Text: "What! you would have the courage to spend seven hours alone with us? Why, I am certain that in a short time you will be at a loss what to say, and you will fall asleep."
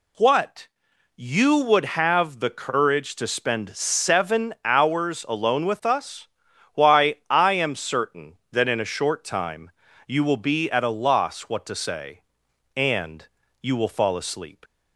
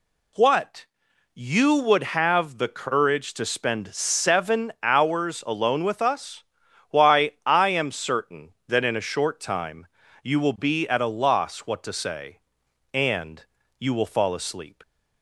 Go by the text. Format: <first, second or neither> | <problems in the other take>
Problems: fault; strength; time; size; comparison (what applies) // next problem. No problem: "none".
neither | pauses between "time" and "you"; slight; the same in both // pauses between "and" and "you"; slight; the same in both